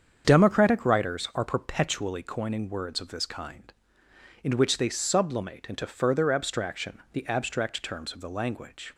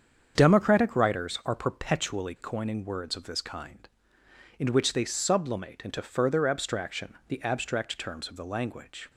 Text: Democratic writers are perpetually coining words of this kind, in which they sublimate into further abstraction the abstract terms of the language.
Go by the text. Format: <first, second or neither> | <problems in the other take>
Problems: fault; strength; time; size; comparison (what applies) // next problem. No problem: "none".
neither | starts louder than the rest; strong; the same in both // pauses between "abstraction" and "the"; slight; the same in both